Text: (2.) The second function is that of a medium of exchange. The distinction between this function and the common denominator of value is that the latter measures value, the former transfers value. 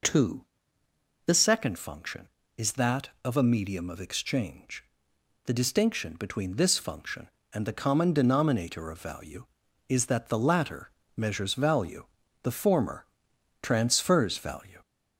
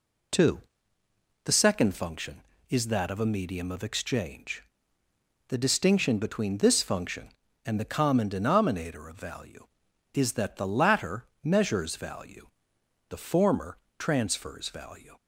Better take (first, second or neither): second